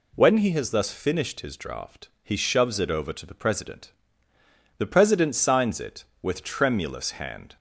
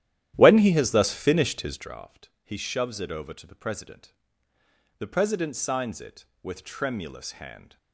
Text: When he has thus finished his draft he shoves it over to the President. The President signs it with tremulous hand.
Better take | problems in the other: first | starts louder than the rest; strong; until 1.9 s; 12 dB

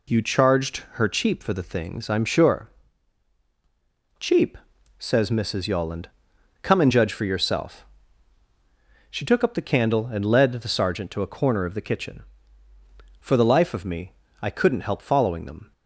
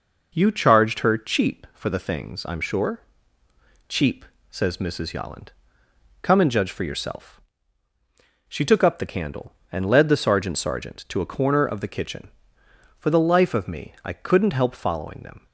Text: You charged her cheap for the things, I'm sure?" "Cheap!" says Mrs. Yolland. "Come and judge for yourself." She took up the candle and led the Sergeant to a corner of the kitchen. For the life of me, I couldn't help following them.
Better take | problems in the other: first | says "Sergeant" twice; at 10.5 s

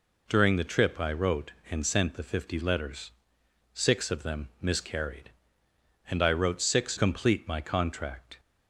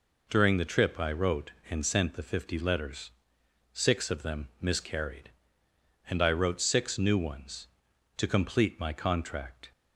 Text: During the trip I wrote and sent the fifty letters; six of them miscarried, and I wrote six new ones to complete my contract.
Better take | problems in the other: second | skips "new ones to"; at 6.9 s

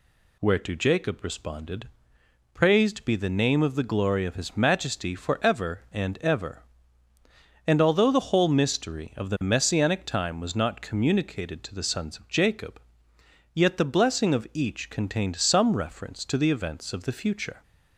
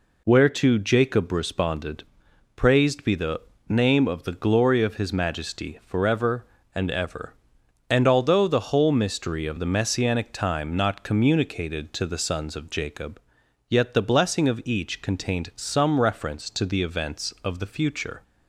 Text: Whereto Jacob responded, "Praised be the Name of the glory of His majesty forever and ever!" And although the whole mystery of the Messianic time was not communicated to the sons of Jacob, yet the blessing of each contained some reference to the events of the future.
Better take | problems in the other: first | pauses between "the" and "Name"; slight; at 3.4 s; 0.28 s long // skips "was"; at 10.7 s

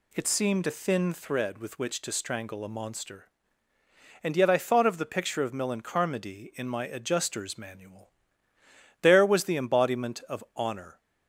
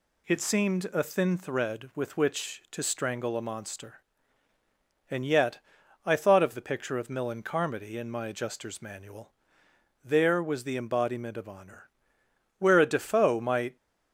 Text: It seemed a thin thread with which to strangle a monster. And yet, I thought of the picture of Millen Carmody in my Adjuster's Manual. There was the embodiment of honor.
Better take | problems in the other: first | goes on to say "Where a Defoe might"; noticeable; from 12.5 s on; 1.1 s long

